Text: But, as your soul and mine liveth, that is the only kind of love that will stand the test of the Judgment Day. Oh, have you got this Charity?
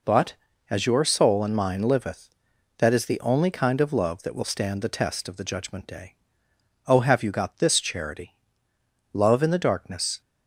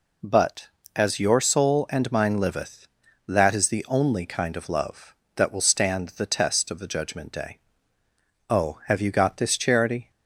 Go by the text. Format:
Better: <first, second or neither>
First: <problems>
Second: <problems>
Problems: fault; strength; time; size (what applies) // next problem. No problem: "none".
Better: second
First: goes on to say "Love in the darkness"; noticeable; from 9.1 s on; 1.0 s long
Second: none